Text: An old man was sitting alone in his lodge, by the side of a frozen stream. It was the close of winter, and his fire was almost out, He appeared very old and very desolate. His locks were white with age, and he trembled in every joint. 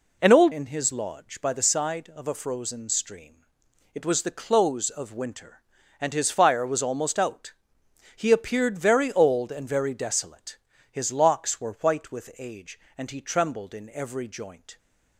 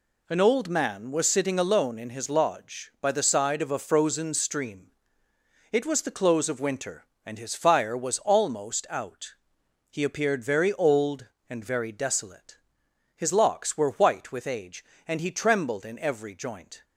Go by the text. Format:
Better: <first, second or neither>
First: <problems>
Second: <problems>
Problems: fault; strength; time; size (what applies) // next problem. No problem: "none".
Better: second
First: skips "man was sitting alone"; at 0.5 s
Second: none